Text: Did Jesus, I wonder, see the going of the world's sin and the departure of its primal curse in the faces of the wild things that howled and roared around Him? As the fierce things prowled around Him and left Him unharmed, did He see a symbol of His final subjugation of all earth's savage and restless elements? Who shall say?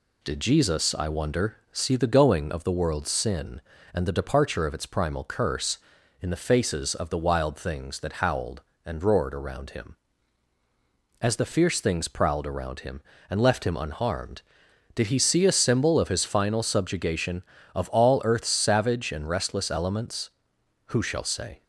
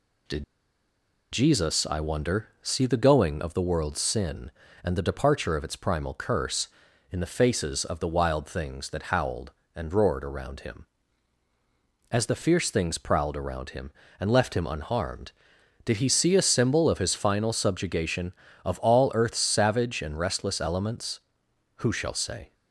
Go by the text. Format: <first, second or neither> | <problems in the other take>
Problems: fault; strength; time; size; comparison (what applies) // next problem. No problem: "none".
first | pauses between "Did" and "Jesus"; noticeable; at 0.4 s; 0.88 s long